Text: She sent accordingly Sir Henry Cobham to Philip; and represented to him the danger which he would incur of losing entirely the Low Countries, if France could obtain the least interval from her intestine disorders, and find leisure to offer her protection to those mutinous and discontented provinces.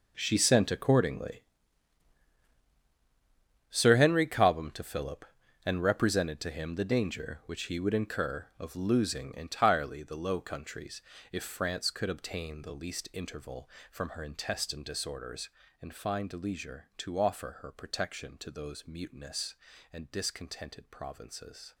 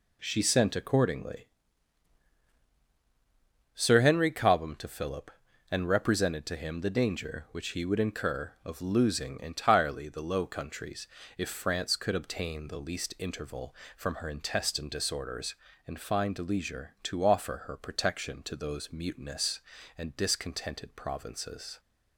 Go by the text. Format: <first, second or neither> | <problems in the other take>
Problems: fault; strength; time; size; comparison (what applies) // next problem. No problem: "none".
second | gets quieter; strong; throughout; 15 dB // pauses between "accordingly" and "Sir"; strong; at 1.4 s; 2.2 s long; strong in the second